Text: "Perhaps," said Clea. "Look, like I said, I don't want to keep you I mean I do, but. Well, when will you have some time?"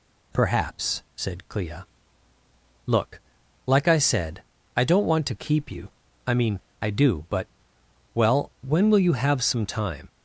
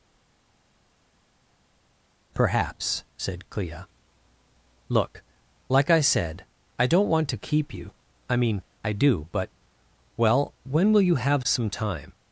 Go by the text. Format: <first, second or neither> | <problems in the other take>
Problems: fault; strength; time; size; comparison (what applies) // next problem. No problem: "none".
first | stays silent before the first word; until 2.3 s; 2.3 s long // pauses between "you" and "I"; slight; at 7.9 s; 0.36 s long; slight in the first // pauses between "mean" and "I"; slight; at 8.6 s; 0.20 s long; slight in the first